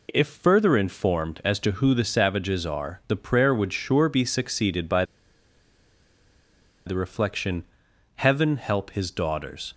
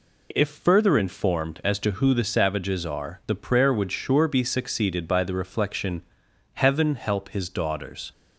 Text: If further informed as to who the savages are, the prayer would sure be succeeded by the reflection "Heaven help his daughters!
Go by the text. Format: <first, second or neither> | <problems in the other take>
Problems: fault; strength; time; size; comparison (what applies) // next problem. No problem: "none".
second | pauses between "by" and "the"; strong; at 5.0 s; 1.8 s long // pauses between "reflection" and "Heaven"; noticeable; at 7.6 s; 0.50 s long; noticeable in the second